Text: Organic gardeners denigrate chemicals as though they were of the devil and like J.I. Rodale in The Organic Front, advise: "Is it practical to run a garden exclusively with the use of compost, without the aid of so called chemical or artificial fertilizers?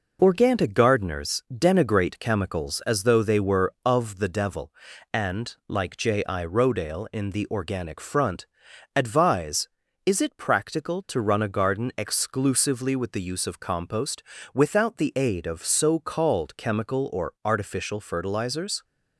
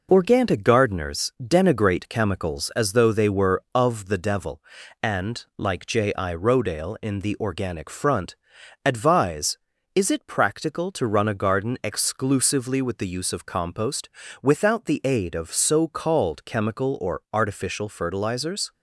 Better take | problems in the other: neither | none

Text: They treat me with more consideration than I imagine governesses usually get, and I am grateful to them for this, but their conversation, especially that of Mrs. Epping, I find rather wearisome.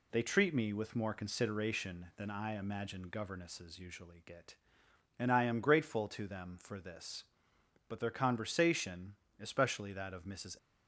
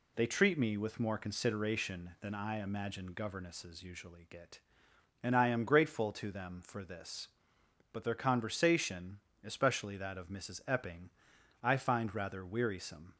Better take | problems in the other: second | stops before "Epping I find rather wearisome"; at 10.5 s

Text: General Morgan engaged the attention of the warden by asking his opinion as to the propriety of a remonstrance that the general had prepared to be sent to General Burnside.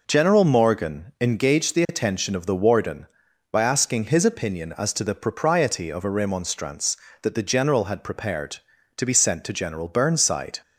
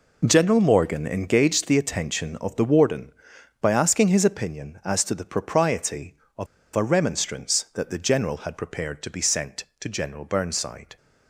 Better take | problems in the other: first | pauses between "of" and "a"; slight; at 6.4 s; 0.29 s long

